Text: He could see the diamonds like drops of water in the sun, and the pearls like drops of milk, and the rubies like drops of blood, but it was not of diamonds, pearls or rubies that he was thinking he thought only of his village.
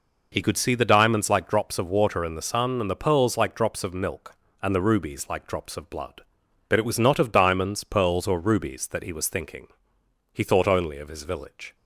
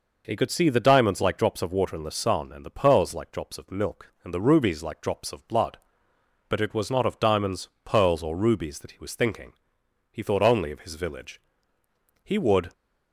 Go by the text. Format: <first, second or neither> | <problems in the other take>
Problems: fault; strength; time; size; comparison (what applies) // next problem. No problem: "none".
first | pauses between "thinking" and "he"; noticeable; at 9.5 s; 0.60 s long; noticeable in the first // goes on to say "He would"; slight; from 12.2 s on; 0.48 s long